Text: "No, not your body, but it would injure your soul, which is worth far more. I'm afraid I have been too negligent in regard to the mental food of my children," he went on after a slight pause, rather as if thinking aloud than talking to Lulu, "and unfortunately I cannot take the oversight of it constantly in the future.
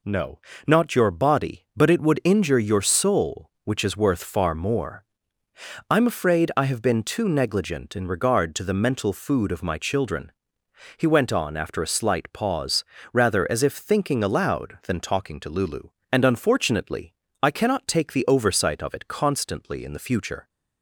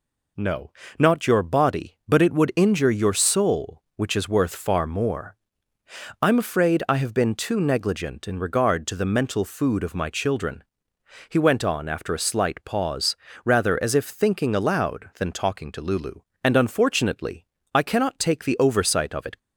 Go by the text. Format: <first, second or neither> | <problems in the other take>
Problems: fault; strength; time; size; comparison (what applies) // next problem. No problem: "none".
first | pauses between "unfortunately" and "I"; slight; at 17.4 s; 0.30 s long; slight in the first // stops before "constantly in the future"; at 19.3 s